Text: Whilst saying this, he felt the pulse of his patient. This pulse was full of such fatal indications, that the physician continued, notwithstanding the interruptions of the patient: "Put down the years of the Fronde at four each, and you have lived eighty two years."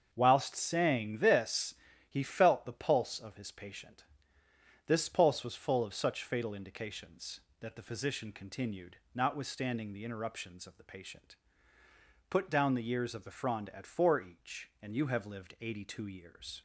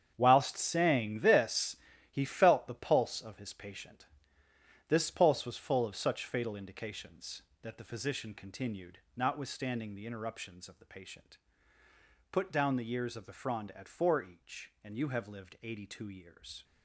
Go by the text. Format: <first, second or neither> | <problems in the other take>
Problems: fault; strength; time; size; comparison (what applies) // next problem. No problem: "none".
first | gets quieter; strong; throughout; 12 dB // starts louder than the rest; strong; until 1.1 s; 8.5 dB; also in the first